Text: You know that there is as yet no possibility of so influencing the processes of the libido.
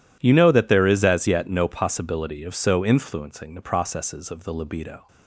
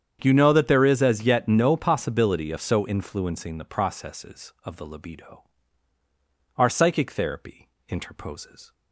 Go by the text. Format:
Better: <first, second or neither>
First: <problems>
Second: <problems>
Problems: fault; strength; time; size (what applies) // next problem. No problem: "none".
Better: first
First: none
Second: starts louder than the rest; strong; until 1.2 s; 8 dB // goes on to say "Our psychic therapy interposes"; strong; from 6.5 s on; 2.1 s long